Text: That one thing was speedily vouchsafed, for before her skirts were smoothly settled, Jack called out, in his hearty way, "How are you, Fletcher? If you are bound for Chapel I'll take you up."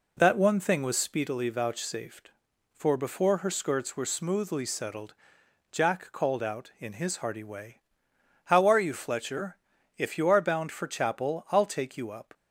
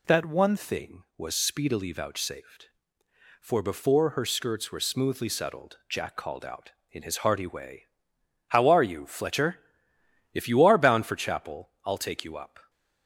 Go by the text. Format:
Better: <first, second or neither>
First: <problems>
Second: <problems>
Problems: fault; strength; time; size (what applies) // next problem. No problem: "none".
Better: first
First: none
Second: changes voice at "thing"; from 0.5 s on; 12.1 s long